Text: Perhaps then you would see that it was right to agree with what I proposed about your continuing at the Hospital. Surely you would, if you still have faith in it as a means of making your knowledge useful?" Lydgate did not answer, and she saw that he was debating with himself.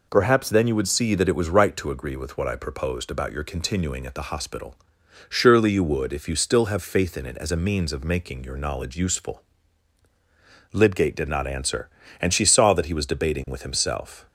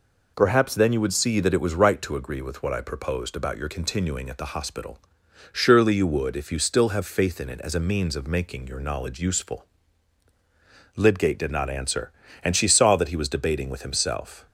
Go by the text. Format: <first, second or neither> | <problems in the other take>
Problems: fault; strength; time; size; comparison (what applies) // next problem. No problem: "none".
neither | none